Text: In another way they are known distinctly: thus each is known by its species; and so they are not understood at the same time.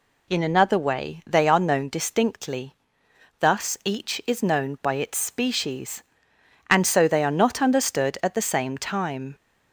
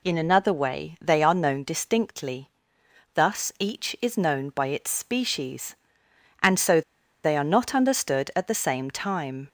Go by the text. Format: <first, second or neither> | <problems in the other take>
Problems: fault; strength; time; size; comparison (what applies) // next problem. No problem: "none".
first | pauses between "so" and "they"; at 6.8 s; 0.42 s long